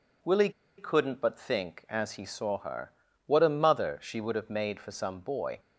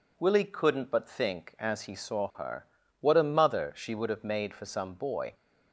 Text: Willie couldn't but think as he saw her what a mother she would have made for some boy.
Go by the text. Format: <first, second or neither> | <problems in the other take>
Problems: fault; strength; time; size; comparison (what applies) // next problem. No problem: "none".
second | pauses between "Willie" and "couldn't"; slight; at 0.5 s; 0.27 s long // pauses between "her" and "what"; slight; at 2.9 s; 0.34 s long; slight in the second